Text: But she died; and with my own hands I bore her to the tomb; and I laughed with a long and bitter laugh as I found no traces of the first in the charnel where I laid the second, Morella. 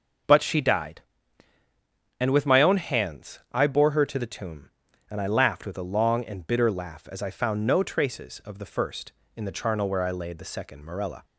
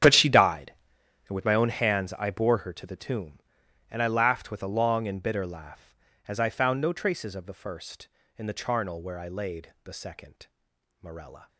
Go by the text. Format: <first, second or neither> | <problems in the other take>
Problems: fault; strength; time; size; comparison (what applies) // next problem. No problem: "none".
first | gets quieter; strong; throughout; 15 dB